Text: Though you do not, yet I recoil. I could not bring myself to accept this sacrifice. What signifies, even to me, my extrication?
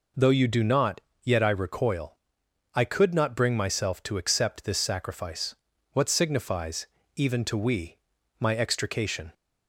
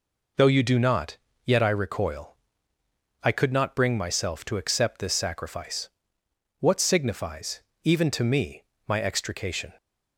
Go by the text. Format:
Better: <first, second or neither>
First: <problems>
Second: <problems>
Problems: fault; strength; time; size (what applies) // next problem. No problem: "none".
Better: second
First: says "we" for "me"; at 7.5 s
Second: none